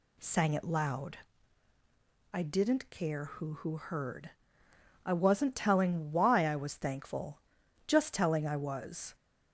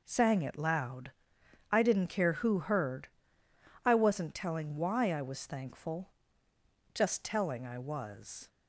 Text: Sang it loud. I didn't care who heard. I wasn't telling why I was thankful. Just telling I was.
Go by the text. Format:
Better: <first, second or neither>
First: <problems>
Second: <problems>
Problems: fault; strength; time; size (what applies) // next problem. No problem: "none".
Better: second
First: says "who" twice; at 3.5 s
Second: none